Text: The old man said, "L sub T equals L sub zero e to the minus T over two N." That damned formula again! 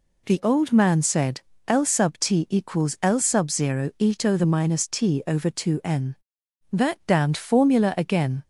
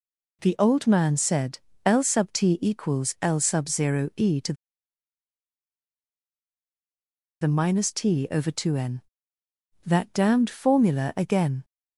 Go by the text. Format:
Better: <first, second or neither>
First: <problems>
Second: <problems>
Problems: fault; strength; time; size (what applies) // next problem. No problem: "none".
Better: first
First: none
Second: pauses between "to" and "the"; strong; at 4.5 s; 2.8 s long